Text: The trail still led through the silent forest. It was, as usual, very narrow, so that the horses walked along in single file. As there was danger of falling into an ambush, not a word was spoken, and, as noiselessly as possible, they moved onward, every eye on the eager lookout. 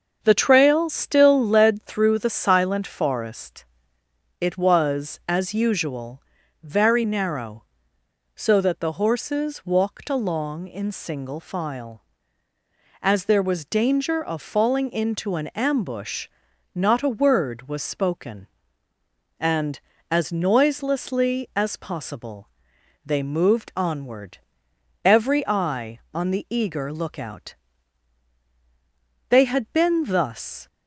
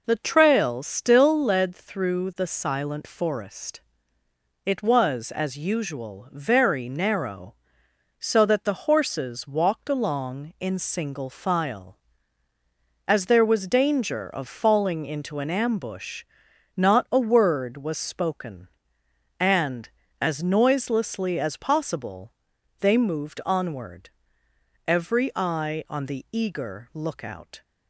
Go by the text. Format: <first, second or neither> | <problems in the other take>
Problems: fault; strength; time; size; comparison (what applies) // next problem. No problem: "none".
second | starts louder than the rest; until 1.2 s; 7 dB // goes on to say "They had been thus"; from 29.2 s on; 1.3 s long